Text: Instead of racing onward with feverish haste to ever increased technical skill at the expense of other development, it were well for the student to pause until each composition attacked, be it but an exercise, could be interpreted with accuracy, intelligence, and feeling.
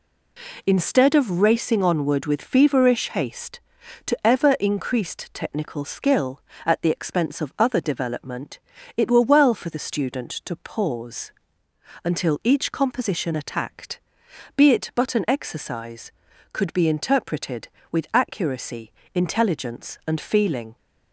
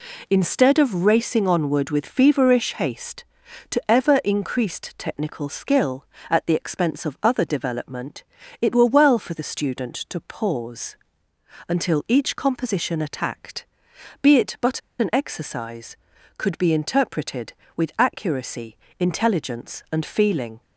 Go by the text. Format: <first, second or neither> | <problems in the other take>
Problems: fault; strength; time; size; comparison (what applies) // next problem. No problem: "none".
first | pauses between "pause" and "until"; noticeable; at 10.9 s; 0.72 s long; noticeable in the first // pauses between "but" and "an"; slight; at 14.7 s; 0.20 s long